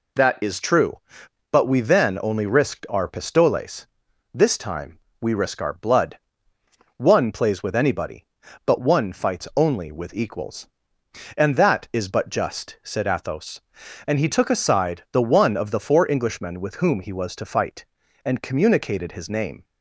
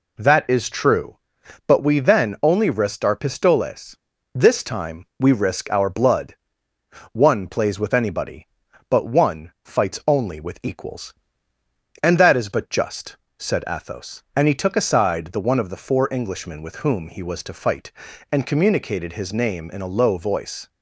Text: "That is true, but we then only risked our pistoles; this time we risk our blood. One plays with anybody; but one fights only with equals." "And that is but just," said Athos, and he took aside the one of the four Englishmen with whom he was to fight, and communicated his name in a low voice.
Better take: second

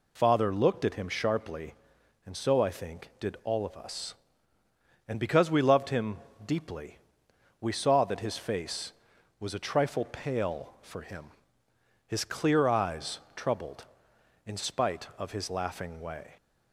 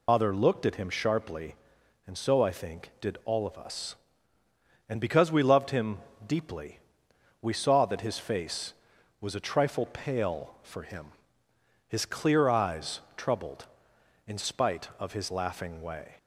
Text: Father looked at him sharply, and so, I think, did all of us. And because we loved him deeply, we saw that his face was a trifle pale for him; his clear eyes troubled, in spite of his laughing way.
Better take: first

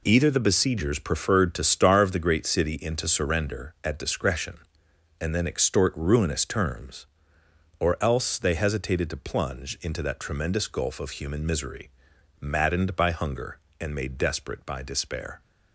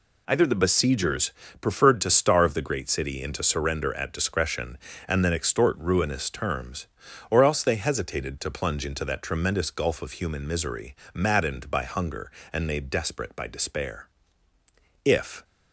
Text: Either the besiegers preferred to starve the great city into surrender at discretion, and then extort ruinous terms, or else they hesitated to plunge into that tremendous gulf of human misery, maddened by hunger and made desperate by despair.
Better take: first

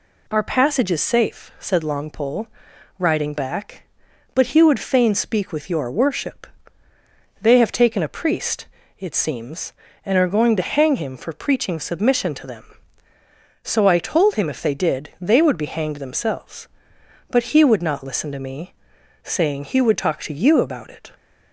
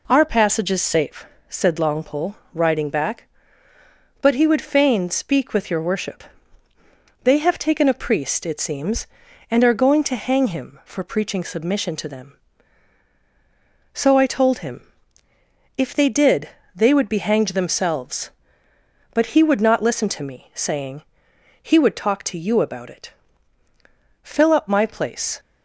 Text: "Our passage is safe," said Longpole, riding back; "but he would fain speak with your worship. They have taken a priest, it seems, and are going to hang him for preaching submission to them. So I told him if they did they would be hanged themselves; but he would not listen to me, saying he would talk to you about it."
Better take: first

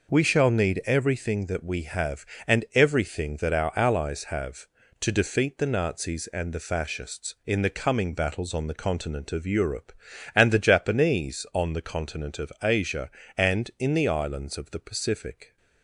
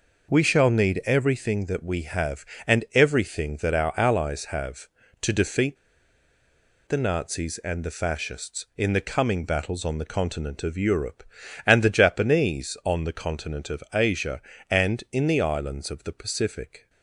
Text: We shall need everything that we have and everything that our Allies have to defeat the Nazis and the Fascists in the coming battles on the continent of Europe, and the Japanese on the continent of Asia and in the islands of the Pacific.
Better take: first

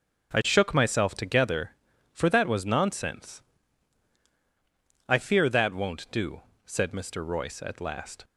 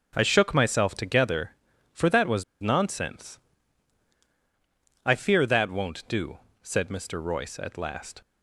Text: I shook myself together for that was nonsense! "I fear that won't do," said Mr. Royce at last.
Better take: first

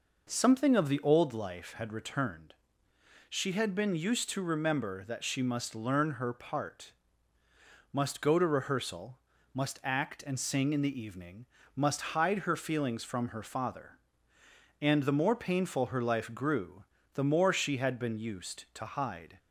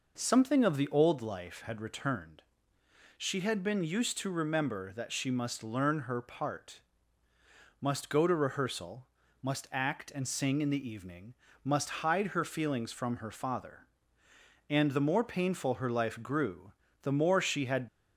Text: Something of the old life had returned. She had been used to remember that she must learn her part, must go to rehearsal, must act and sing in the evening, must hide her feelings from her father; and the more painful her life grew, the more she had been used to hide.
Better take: first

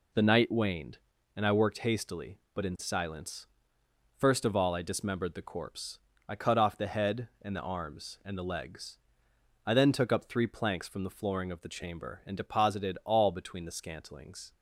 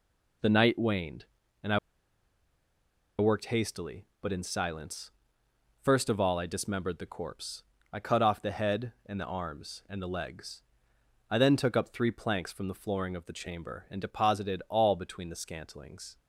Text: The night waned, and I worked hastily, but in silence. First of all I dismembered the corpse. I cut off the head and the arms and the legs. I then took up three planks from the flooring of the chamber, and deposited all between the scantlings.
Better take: first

